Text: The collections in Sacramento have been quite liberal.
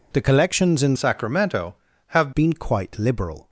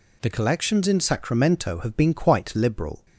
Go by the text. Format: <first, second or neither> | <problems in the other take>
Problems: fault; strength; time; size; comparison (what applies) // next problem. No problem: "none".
second | changes voice from "Sacramento" to "have"; from 0.9 to 2.3 s; 1.4 s long